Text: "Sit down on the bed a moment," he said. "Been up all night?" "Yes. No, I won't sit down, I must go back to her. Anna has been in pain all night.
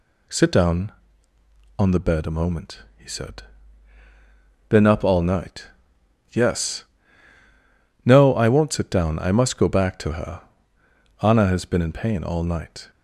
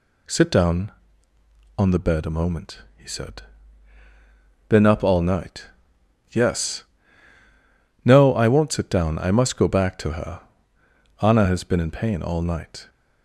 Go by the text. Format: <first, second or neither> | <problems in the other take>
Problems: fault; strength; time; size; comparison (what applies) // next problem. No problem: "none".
neither | none